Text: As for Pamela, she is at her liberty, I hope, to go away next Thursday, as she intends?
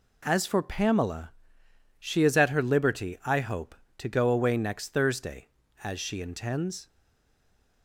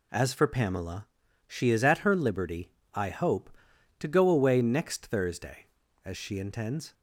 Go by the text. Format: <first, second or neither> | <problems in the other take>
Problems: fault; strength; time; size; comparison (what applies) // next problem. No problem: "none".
second | stays silent after the last word; from 6.8 s on; 1.0 s long